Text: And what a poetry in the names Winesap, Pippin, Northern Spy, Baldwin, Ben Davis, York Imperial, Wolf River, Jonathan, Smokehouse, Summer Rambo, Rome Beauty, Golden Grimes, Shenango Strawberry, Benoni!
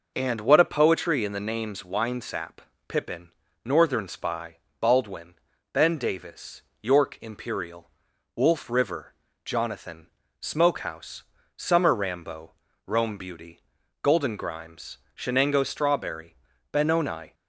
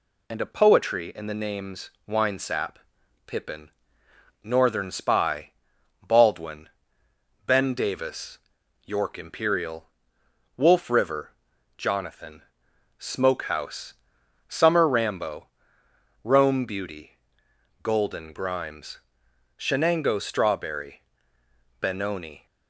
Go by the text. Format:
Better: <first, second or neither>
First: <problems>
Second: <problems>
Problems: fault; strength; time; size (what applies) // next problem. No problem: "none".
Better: first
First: none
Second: skips "what"; at 0.4 s // pauses between "names" and "Winesap"; slight; at 1.9 s; 0.18 s long